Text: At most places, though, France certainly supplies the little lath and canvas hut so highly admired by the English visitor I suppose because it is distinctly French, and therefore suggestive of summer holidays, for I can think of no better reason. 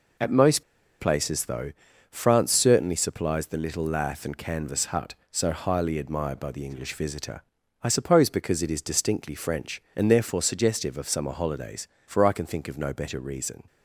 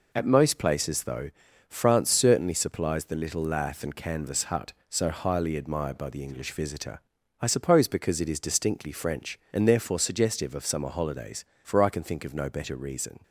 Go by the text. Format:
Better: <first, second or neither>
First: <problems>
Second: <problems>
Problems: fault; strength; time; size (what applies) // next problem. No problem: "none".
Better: second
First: pauses between "most" and "places"; at 0.6 s; 0.36 s long // pauses between "visitor" and "I"; at 7.4 s; 0.40 s long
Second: pauses between "visitor" and "I"; at 7.0 s; 0.40 s long